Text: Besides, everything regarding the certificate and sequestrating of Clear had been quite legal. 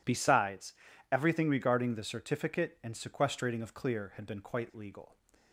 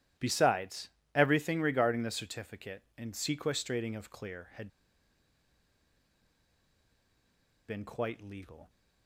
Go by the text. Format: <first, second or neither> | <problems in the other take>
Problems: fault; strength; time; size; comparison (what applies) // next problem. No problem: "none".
first | starts louder than the rest; strong; until 1.4 s; 13 dB // pauses between "had" and "been"; strong; at 4.6 s; 3.0 s long